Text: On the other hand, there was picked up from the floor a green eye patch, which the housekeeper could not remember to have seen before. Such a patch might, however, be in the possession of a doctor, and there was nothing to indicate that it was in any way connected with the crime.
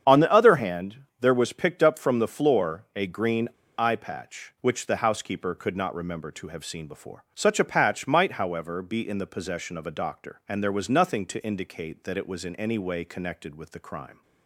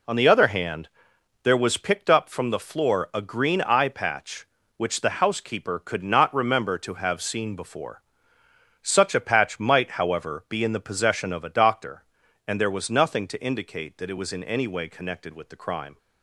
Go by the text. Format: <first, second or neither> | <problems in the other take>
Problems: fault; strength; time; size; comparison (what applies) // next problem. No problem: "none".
second | starts louder than the rest; strong; until 1.2 s; 8 dB // pauses between "green" and "eye"; slight; at 3.4 s; 0.28 s long